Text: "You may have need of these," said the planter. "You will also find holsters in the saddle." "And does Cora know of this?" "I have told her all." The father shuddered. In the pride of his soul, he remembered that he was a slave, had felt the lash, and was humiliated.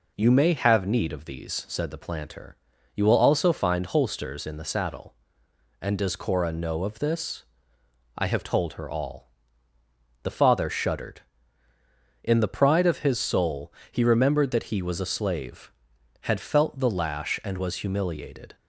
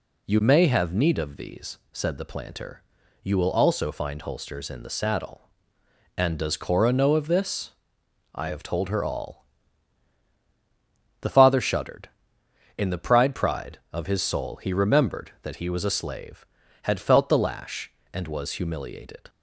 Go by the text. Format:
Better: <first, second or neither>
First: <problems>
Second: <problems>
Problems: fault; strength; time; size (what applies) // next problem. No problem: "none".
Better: first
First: none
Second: says "pride" twice; at 13.3 s